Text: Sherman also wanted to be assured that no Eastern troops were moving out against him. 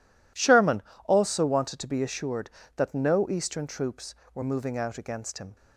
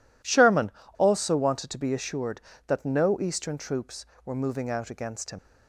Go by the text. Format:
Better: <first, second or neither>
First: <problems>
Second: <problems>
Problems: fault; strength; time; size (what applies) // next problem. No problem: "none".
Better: first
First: pauses between "Sherman" and "also"; slight; at 0.8 s; 0.22 s long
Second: pauses between "Sherman" and "also"; slight; at 0.7 s; 0.26 s long // leaves "him" unfinished; at 5.3 s; 80 ms